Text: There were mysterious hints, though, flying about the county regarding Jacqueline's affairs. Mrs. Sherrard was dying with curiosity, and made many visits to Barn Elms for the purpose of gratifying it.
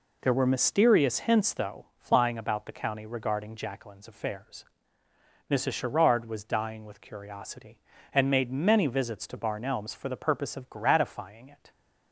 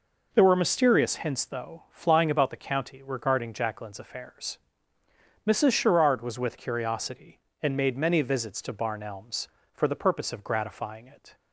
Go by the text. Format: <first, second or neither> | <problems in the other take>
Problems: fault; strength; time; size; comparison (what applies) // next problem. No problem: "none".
first | skips "dying"; at 6.3 s